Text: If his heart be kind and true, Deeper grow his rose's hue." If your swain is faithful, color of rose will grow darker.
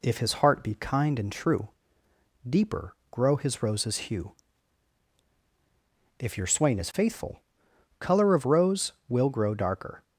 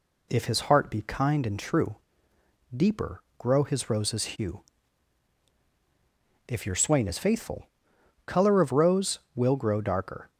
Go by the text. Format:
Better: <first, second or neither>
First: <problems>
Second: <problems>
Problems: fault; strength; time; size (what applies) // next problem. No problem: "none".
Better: neither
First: pauses between "Deeper" and "grow"; slight; at 2.9 s; 0.16 s long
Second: pauses between "Deeper" and "grow"; slight; at 3.2 s; 0.16 s long